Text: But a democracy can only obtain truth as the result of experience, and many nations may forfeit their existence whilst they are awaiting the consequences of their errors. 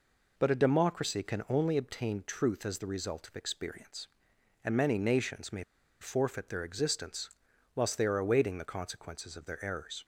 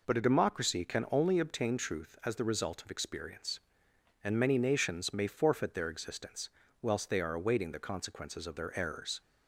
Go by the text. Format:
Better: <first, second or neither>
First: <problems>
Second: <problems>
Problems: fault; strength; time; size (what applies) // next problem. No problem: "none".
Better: second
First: pauses between "may" and "forfeit"; at 5.6 s; 0.37 s long // pauses between "existence" and "whilst"; noticeable; at 7.2 s; 0.46 s long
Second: pauses between "existence" and "whilst"; slight; at 6.4 s; 0.32 s long